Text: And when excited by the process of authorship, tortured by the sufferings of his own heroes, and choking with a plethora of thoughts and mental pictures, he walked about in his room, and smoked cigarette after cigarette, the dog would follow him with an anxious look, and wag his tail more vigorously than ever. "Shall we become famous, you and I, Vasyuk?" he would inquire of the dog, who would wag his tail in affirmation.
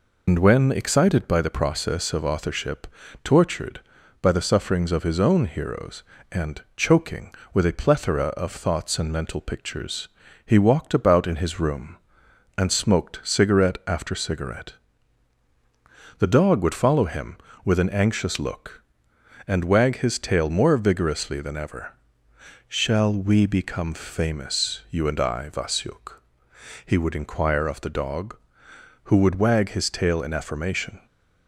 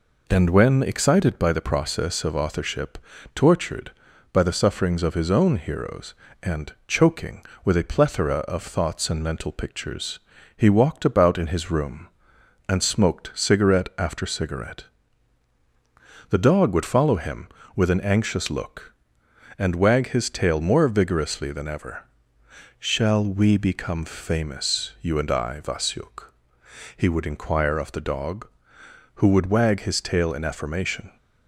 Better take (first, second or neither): second